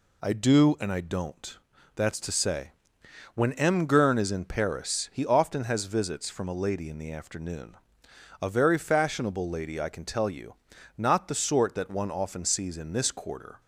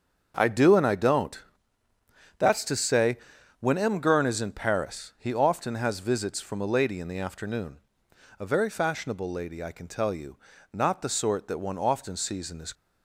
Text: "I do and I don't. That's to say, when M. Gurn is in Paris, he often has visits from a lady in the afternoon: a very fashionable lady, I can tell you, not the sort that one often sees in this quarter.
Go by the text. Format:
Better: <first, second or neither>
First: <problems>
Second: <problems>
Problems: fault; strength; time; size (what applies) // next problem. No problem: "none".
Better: first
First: none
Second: starts louder than the rest; until 1.3 s; 7 dB // stops before "quarter"; at 12.7 s